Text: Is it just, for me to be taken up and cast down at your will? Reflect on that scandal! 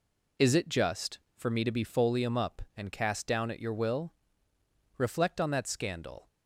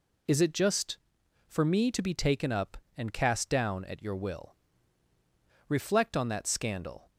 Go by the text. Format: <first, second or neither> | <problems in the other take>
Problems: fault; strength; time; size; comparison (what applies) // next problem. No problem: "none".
second | says "folium" for "taken"; at 1.8 s